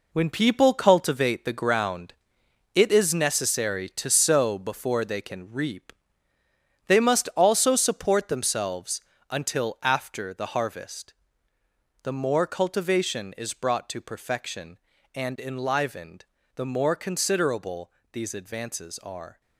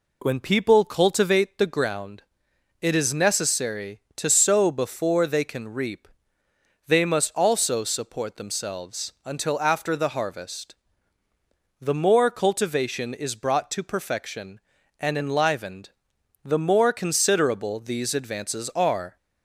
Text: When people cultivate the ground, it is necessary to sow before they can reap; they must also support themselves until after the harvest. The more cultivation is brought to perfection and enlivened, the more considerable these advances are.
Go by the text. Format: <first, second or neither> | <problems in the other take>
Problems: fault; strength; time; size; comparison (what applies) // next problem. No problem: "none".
second | gets quieter; strong; throughout; 9.5 dB // pauses between "themselves" and "until"; slight; at 9.0 s; 0.30 s long // pauses between "considerable" and "these"; slight; at 17.9 s; 0.22 s long